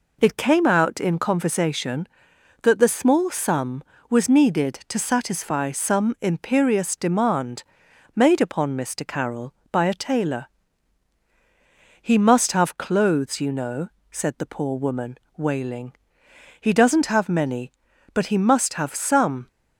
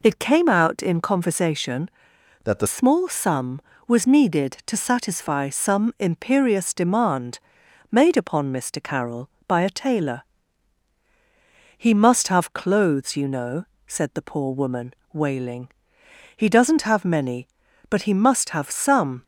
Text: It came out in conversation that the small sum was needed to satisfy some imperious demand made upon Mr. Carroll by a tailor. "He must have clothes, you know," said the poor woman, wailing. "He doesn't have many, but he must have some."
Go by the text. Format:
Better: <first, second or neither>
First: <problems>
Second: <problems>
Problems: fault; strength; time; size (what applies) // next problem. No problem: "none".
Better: first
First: pauses between "demand" and "made"; noticeable; at 7.6 s; 0.50 s long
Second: changes voice from "that" to "the"; from 2.4 to 2.6 s; 0.2 s long // pauses between "demand" and "made"; noticeable; at 7.3 s; 0.50 s long